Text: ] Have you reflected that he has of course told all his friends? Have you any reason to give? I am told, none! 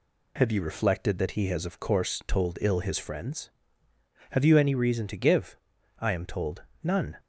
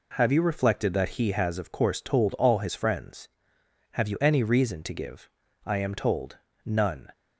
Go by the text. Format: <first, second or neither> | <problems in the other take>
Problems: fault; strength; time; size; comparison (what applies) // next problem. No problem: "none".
second | says "ill" for "all"; at 2.6 s